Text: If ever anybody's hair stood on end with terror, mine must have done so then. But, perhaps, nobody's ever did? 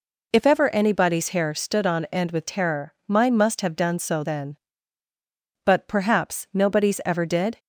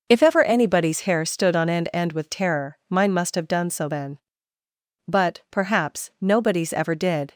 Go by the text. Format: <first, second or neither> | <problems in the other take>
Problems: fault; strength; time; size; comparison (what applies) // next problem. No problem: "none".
first | says "end" twice; at 1.9 s